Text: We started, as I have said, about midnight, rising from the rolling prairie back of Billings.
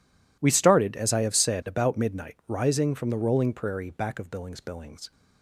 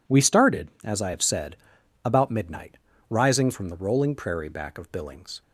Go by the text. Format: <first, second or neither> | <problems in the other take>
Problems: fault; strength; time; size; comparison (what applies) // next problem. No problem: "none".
second | says "Billings" twice; at 4.6 s